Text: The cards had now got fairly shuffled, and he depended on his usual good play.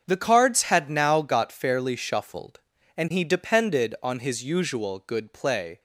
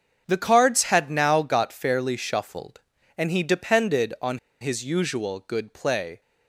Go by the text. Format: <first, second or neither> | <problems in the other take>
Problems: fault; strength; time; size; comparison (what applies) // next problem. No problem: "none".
first | starts louder than the rest; until 1.2 s; 7 dB; also in the first // pauses between "on" and "his"; slight; at 4.3 s; 0.22 s long